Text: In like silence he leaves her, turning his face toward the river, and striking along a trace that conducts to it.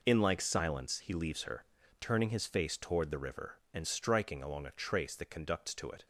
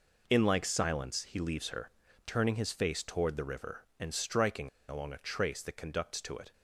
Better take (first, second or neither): first